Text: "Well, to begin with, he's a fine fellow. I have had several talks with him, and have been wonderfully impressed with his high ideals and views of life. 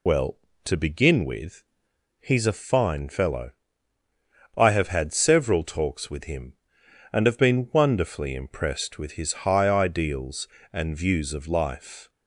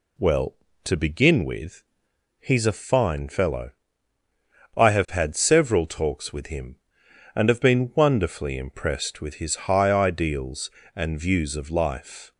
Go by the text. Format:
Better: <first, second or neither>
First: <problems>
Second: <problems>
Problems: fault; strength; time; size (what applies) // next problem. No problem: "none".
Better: second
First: loses the start of "Well"; at 0.0 s; 50 ms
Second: none